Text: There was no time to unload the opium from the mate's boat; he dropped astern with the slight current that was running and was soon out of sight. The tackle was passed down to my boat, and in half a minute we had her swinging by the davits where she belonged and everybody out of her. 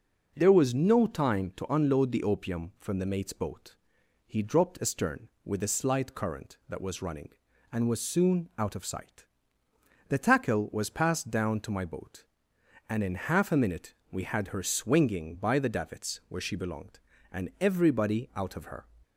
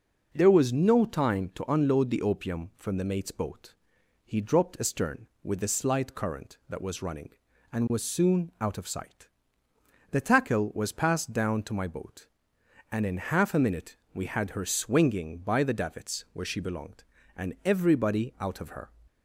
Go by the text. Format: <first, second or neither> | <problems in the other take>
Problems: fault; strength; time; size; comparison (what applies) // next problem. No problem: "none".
neither | pauses between "minute" and "we"; slight; the same in both